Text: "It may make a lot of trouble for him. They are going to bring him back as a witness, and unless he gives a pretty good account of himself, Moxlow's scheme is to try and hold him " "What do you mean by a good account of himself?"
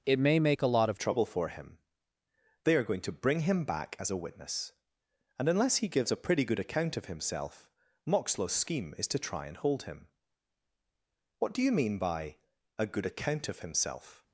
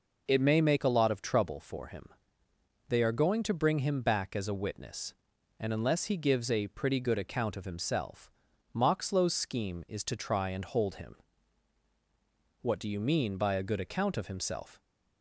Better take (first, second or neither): second